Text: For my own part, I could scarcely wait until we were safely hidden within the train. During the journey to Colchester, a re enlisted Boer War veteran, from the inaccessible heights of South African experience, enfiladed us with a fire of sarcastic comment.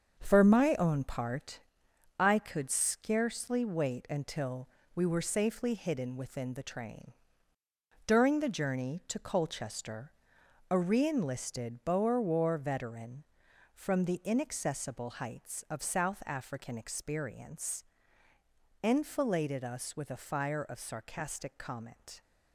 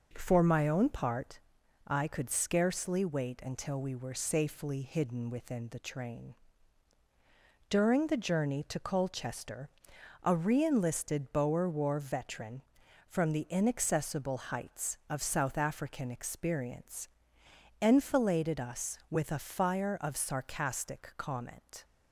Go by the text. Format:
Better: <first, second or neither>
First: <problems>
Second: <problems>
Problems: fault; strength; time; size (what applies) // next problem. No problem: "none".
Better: second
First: gets quieter; throughout; 7 dB // pauses between "until" and "we"; slight; at 4.6 s; 0.28 s long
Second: none